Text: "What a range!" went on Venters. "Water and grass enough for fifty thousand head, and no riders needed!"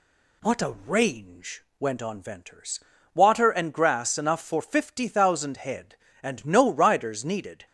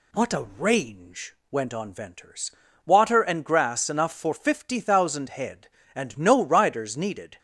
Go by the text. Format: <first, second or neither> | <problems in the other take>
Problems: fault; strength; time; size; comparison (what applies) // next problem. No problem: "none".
neither | none